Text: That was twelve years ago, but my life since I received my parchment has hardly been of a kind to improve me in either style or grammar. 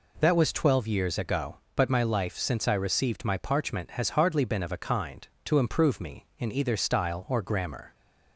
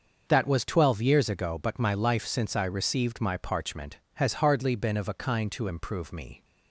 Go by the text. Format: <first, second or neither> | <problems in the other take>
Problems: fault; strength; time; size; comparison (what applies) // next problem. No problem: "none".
first | starts louder than the rest; until 1.2 s; 6.5 dB // stops before "in either style or grammar"; at 6.4 s